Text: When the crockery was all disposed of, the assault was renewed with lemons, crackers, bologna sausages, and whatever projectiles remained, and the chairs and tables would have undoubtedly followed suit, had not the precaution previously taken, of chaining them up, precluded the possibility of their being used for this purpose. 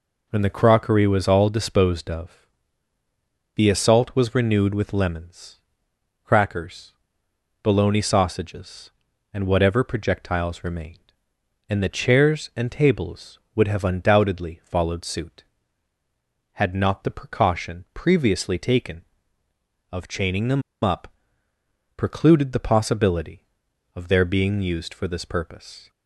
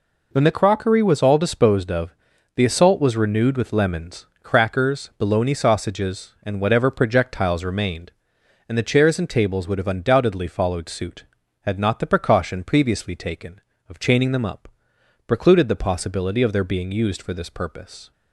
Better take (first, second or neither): second